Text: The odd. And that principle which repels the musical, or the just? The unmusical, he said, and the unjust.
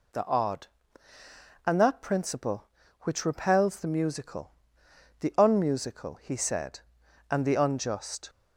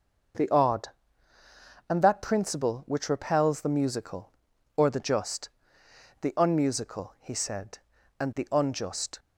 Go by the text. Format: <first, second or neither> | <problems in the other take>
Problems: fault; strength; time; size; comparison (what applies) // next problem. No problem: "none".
second | skips "or the just"; at 4.8 s